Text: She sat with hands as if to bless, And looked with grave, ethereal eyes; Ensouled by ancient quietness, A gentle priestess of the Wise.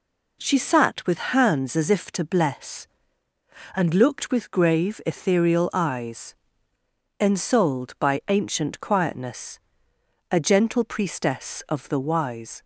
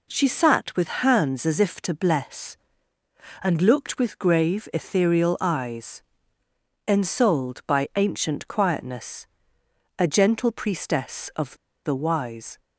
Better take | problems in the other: first | pauses between "of" and "the"; slight; at 11.5 s; 0.30 s long

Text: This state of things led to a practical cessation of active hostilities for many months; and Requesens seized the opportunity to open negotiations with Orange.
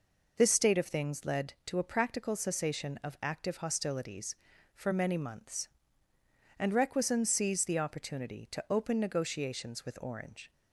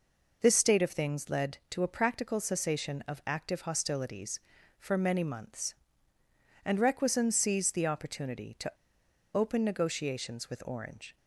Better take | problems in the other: first | pauses between "to" and "open"; noticeable; at 8.6 s; 0.64 s long

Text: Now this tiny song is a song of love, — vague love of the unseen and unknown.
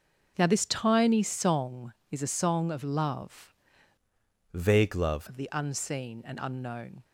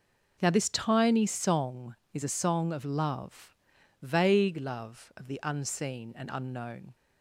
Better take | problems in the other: second | changes voice from "vague" to "love"; from 4.5 to 5.2 s; 0.7 s long

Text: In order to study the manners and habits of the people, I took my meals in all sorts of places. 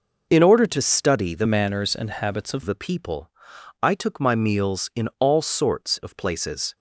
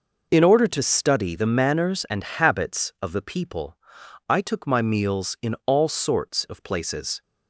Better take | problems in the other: second | changes voice from "manners" to "of"; from 1.4 to 2.6 s; 1.2 s long

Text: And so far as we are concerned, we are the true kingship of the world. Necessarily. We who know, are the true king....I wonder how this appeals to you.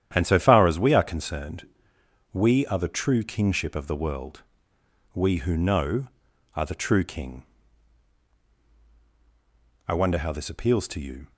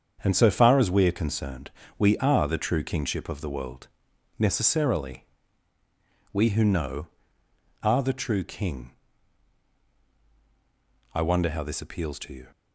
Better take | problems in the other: second | starts louder than the rest; strong; until 1.1 s; 10 dB; strong in the second // skips "Necessarily"; at 4.7 s

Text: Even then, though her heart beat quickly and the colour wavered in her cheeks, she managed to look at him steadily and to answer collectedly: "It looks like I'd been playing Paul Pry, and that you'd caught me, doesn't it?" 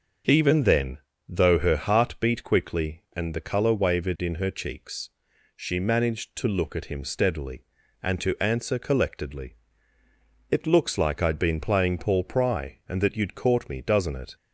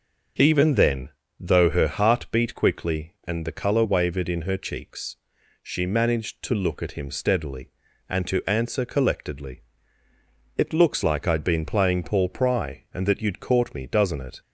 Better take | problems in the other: neither | starts louder than the rest; the same in both

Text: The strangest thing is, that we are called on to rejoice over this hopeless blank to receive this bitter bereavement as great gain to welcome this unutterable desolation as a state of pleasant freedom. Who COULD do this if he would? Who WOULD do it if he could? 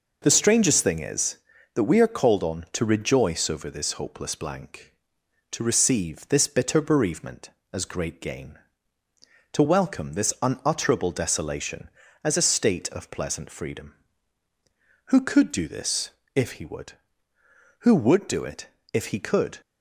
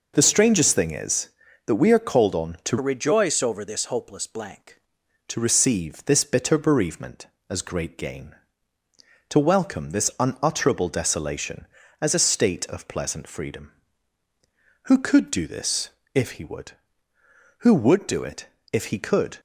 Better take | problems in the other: first | changes voice from "rejoice" to "blank"; from 2.8 to 4.7 s; 1.9 s long // pauses between "this" and "if"; slight; at 15.8 s; 0.24 s long; slight in the first // pauses between "it" and "if"; slight; at 18.4 s; 0.26 s long; slight in the first

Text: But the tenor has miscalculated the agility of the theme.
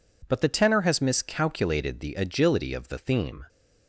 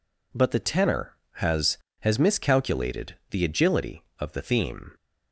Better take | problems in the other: first | says "has" twice; at 2.0 s // pauses between "miscalculated" and "the"; slight; at 3.1 s; 0.16 s long

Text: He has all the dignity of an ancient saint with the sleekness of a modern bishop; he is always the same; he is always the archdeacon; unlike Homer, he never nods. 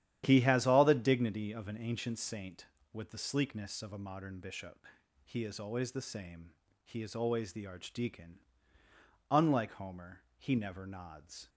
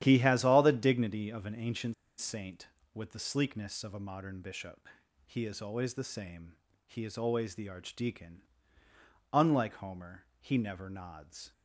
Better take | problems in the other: first | starts louder than the rest; strong; until 1.0 s; 11 dB; strong in the first // pauses between "ancient" and "saint"; slight; at 1.9 s; 0.23 s long

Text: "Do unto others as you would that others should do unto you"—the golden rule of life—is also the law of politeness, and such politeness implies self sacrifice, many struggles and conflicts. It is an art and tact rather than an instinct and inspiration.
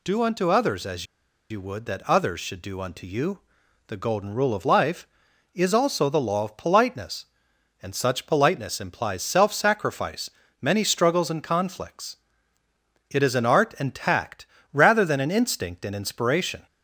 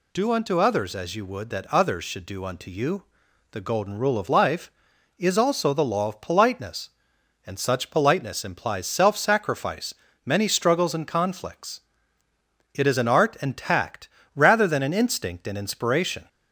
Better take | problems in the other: second | pauses between "as" and "you"; at 1.0 s; 0.45 s long // pauses between "tact" and "rather"; slight; at 14.4 s; 0.28 s long; slight in the second

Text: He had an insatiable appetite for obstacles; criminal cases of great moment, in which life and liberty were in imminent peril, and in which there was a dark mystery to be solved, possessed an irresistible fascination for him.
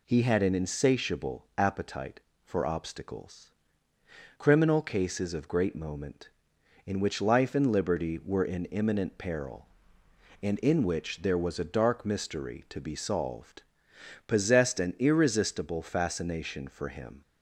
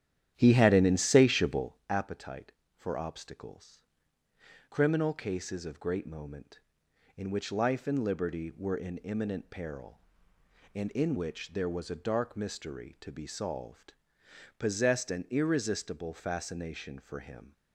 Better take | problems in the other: first | starts louder than the rest; strong; until 1.9 s; 11 dB

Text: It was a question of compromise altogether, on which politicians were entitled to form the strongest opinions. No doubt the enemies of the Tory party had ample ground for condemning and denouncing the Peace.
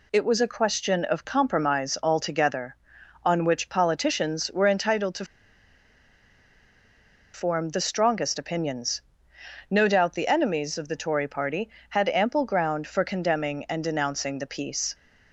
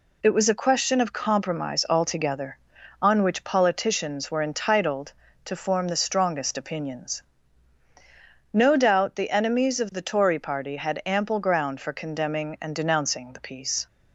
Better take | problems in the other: second | pauses between "to" and "form"; strong; at 5.2 s; 2.0 s long

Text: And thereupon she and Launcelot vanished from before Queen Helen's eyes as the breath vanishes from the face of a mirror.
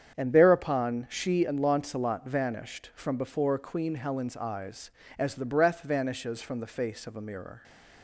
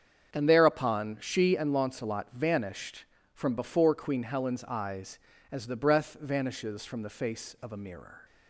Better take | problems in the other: neither | starts louder than the rest; strong; the same in both

